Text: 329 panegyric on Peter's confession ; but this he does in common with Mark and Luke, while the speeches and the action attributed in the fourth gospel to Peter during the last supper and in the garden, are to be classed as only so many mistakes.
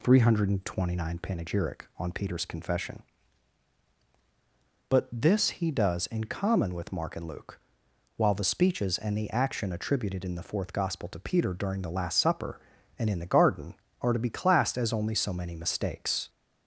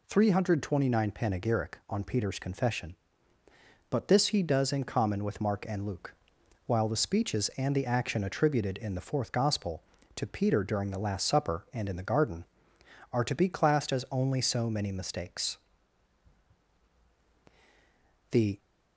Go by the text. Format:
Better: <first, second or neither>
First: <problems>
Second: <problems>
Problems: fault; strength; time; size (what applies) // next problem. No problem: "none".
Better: first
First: none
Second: goes on to say "The"; slight; from 18.3 s on; 0.28 s long